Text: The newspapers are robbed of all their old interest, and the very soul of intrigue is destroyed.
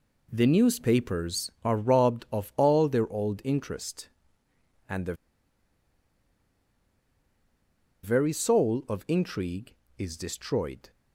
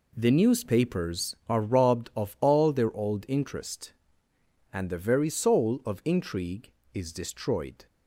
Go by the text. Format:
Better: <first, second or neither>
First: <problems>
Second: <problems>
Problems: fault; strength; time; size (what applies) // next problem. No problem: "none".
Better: second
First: pauses between "the" and "very"; strong; at 5.1 s; 2.8 s long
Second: none